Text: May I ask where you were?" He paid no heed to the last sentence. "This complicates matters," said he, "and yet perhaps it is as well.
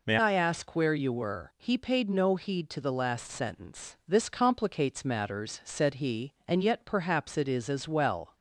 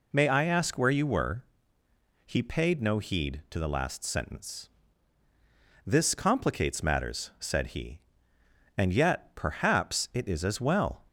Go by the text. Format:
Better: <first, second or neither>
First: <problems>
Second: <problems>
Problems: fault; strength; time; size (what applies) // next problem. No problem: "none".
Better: second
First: changes voice at "I"; from 0.1 s on; 8.2 s long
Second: none